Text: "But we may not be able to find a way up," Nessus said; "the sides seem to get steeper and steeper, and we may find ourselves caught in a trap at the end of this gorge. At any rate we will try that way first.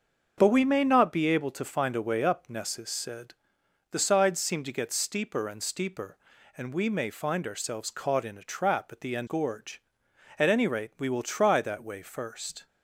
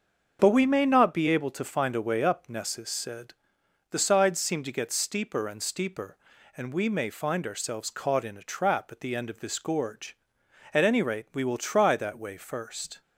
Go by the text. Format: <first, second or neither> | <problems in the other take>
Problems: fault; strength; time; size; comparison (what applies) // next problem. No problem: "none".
second | starts louder than the rest; until 1.3 s; 6.5 dB; also in the second // skips "of this"; at 9.2 s